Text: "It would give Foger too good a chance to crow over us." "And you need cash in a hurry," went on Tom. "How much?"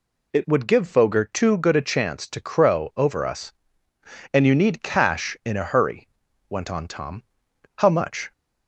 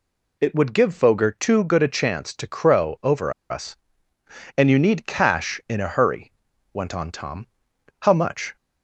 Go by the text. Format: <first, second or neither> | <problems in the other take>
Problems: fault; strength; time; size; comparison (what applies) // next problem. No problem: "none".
first | pauses between "over" and "us"; slight; at 3.3 s; 0.17 s long